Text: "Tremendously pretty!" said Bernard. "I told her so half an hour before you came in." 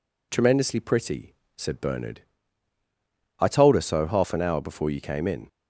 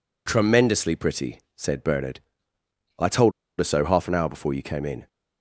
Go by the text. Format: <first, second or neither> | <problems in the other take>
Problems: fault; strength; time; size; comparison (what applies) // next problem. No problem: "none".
first | pauses between "told" and "her"; slight; at 3.3 s; 0.27 s long